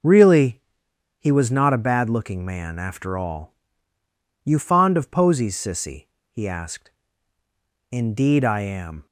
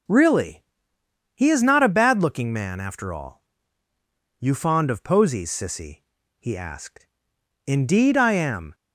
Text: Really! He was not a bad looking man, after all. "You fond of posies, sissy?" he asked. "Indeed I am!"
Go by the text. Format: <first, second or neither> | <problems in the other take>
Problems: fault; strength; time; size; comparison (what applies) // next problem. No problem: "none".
first | says "is" for "was"; at 1.4 s